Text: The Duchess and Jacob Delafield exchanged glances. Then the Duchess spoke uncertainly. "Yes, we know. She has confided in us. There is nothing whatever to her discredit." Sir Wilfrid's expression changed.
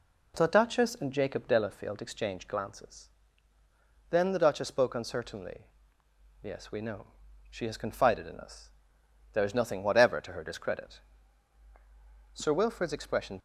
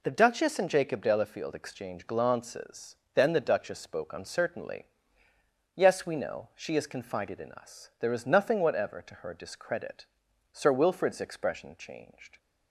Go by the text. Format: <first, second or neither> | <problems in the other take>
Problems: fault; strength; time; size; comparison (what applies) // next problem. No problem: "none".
second | stops before "changed"; at 13.3 s